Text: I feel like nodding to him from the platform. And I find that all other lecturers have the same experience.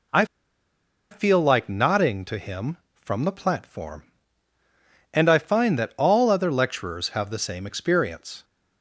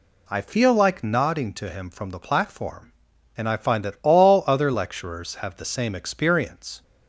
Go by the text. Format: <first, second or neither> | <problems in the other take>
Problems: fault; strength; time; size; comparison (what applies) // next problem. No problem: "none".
second | pauses between "I" and "feel"; noticeable; at 0.2 s; 0.86 s long